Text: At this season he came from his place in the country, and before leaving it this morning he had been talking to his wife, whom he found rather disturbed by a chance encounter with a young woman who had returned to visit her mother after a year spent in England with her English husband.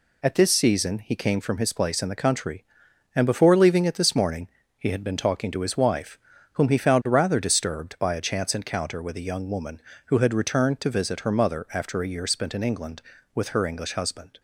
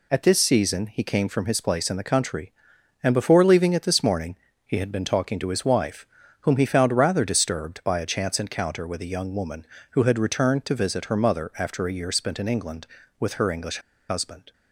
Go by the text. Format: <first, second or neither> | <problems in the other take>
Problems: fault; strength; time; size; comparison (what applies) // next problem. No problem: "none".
first | pauses between "morning" and "he"; slight; at 4.3 s; 0.30 s long; slight in the first // pauses between "English" and "husband"; slight; at 13.7 s; 0.30 s long